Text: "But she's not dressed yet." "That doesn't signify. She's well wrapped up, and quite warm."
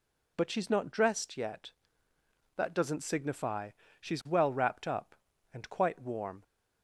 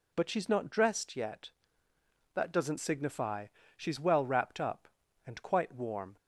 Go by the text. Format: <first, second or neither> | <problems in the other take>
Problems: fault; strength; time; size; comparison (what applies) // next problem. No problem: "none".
neither | none